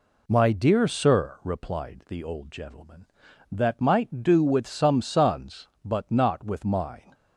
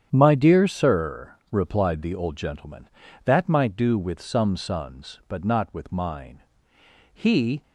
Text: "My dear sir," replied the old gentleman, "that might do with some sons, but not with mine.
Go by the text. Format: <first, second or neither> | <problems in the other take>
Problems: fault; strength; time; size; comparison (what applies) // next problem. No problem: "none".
first | starts louder than the rest; strong; until 1.1 s; 9 dB // goes on to say "He"; slight; from 7.1 s on; 0.48 s long